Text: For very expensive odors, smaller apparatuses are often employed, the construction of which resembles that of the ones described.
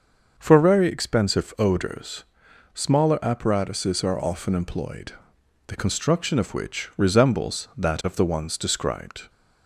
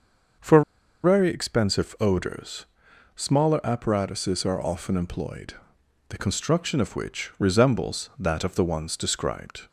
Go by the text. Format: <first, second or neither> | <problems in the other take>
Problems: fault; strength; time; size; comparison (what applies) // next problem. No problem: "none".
first | starts louder than the rest; until 1.8 s; 6.5 dB; also in the first // pauses between "For" and "very"; at 0.6 s; 0.41 s long